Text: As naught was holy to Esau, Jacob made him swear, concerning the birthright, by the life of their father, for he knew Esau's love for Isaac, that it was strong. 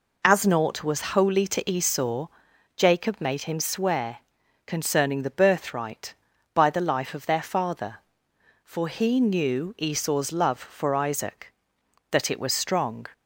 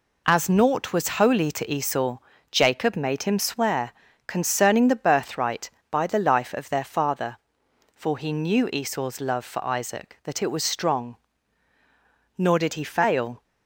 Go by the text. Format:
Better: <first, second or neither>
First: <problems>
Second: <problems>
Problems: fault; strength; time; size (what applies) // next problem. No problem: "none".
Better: first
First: none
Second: goes on to say "Nor did he fail"; noticeable; from 12.3 s on; 1.0 s long